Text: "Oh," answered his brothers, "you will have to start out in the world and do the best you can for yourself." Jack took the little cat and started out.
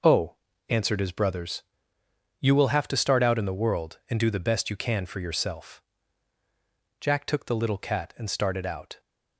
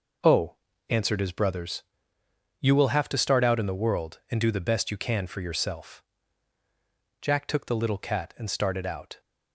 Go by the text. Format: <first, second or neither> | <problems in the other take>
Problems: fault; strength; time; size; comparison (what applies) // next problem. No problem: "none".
neither | none